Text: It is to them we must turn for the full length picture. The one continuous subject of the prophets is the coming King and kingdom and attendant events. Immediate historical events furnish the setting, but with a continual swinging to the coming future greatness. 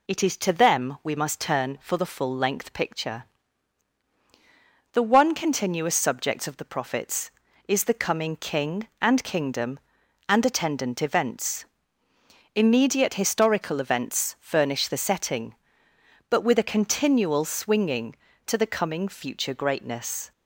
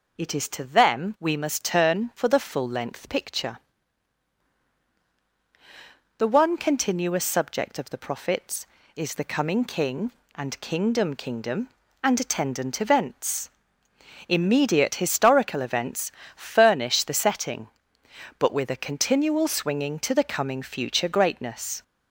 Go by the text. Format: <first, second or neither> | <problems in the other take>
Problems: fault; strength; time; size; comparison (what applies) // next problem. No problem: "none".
first | says "kingdom" twice; at 11.1 s // pauses between "events" and "furnish"; slight; at 16.1 s; 0.24 s long